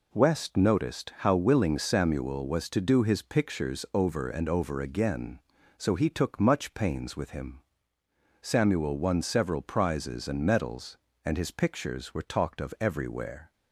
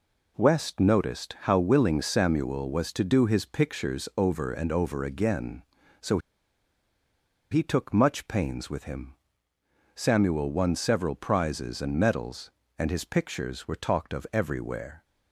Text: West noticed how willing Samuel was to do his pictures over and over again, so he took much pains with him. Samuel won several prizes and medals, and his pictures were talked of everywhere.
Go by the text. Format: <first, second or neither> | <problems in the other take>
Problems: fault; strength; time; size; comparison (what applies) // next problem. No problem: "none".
first | pauses between "so" and "he"; strong; at 6.1 s; 1.3 s long